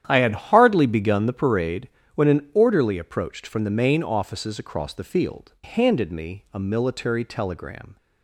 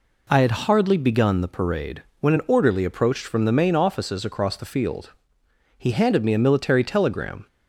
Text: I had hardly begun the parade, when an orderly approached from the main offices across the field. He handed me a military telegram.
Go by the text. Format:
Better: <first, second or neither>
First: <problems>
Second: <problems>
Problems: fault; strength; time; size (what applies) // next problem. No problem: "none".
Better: second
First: starts louder than the rest; strong; until 1.0 s; 10 dB // skips "He"; at 5.5 s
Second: none